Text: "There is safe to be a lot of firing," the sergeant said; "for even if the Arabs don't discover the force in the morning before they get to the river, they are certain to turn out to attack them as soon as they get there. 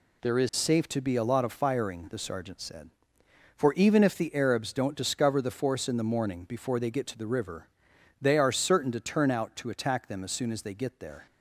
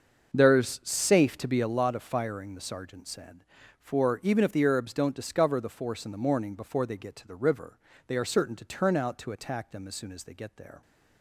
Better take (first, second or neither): first